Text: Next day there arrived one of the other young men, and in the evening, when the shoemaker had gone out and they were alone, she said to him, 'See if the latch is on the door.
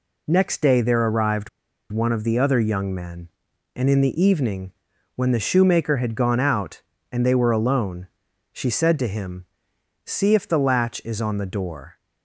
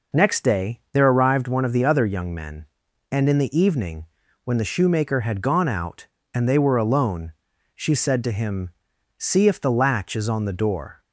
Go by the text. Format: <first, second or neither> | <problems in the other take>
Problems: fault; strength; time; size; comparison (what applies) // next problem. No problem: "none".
second | pauses between "arrived" and "one"; at 1.4 s; 0.41 s long